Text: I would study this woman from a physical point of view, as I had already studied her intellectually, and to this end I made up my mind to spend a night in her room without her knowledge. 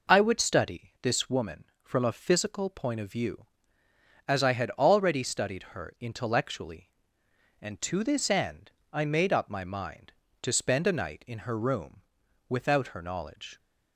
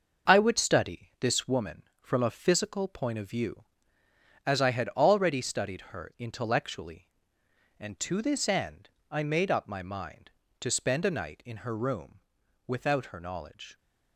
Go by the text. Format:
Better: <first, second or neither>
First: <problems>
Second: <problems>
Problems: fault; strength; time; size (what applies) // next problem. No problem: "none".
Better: first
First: pauses between "end" and "I"; slight; at 8.7 s; 0.22 s long // pauses between "room" and "without"; at 12.0 s; 0.44 s long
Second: gets quieter; strong; throughout; 7 dB // pauses between "end" and "I"; slight; at 8.8 s; 0.22 s long // pauses between "room" and "without"; at 12.2 s; 0.44 s long